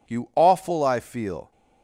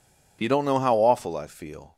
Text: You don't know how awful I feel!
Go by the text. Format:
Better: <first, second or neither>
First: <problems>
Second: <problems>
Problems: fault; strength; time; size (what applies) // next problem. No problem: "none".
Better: second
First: skips "don't know how"; at 0.3 s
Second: none